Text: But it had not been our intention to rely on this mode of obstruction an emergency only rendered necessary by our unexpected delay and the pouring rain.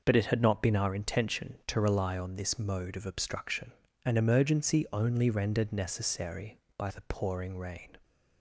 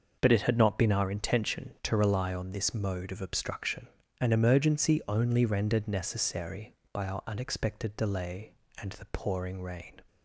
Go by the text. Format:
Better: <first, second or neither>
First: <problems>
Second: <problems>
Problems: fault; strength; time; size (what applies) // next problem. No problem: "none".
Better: second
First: pauses between "obstruction" and "an"; slight; at 3.7 s; 0.34 s long // skips "our unexpected delay and"; at 6.8 s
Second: pauses between "obstruction" and "an"; slight; at 3.8 s; 0.34 s long